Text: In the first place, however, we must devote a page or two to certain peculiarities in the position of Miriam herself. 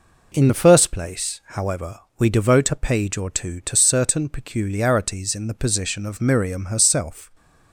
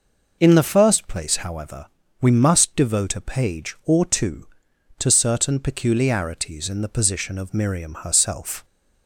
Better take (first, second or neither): second